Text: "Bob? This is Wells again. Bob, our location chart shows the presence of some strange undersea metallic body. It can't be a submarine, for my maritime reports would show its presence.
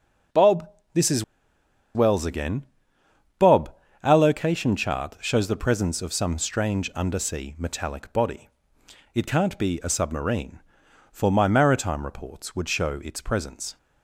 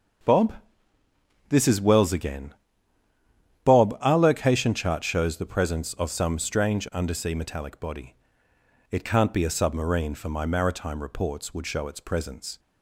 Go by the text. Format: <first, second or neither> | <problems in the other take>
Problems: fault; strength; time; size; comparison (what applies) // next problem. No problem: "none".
second | starts louder than the rest; until 2.2 s; 6.5 dB; also in the second // pauses between "is" and "Wells"; noticeable; at 1.2 s; 0.70 s long